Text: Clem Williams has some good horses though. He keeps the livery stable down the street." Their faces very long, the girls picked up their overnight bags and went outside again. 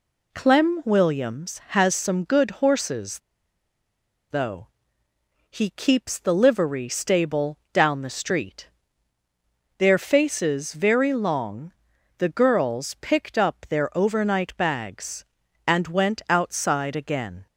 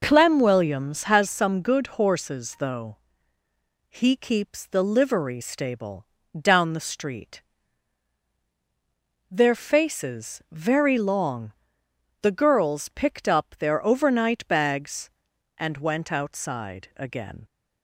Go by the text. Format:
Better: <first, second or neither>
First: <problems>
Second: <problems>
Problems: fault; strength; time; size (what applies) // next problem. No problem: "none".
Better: second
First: pauses between "horses" and "though"; at 3.1 s; 1.1 s long // pauses between "stable" and "down"; slight; at 7.5 s; 0.16 s long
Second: pauses between "stable" and "down"; slight; at 6.0 s; 0.26 s long